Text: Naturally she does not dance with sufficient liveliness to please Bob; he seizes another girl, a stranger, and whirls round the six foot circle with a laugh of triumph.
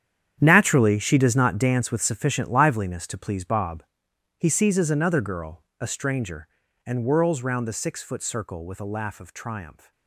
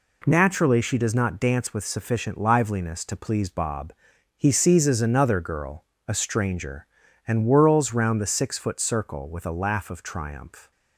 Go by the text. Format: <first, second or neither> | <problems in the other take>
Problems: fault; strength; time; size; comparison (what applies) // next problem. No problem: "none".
second | gets quieter; strong; throughout; 14 dB